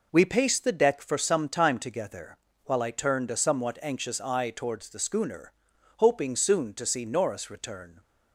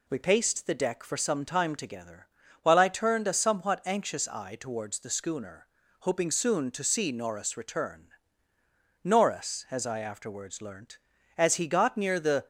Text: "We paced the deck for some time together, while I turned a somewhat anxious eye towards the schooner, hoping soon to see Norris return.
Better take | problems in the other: first | goes on to say "Norris as I afterwards learnt as he got near the"; strong; from 9.0 s on; 3.4 s long

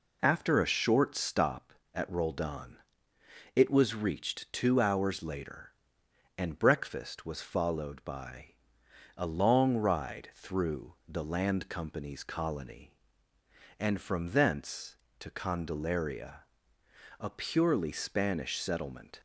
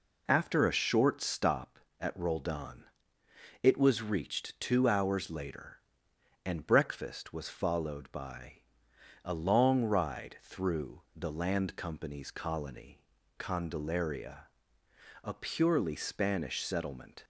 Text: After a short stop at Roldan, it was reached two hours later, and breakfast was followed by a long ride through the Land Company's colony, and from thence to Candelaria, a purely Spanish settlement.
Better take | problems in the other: first | pauses between "by" and "a"; noticeable; at 8.6 s; 0.62 s long; noticeable in the first // skips "and from thence to"; at 13.1 s

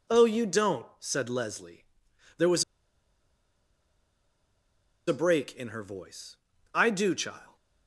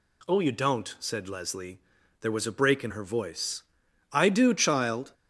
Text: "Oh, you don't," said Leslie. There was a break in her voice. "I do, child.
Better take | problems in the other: second | pauses between "was" and "a"; strong; at 2.6 s; 2.4 s long

